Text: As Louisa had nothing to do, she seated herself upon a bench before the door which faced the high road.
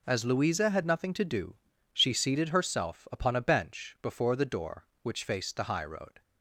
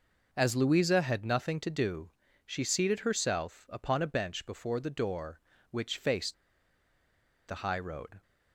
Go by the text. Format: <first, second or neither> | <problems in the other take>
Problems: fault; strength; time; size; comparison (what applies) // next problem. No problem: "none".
first | pauses between "faced" and "the"; at 6.3 s; 1.1 s long